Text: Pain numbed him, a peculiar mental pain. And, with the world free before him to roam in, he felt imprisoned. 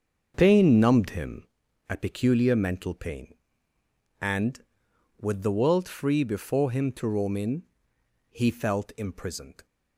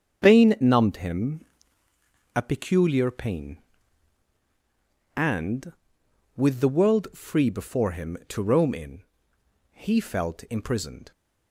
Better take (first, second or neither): first